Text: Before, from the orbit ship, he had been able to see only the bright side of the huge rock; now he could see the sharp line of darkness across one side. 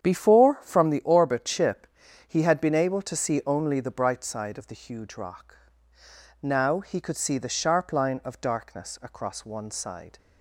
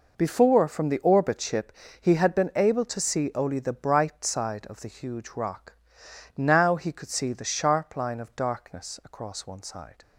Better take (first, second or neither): second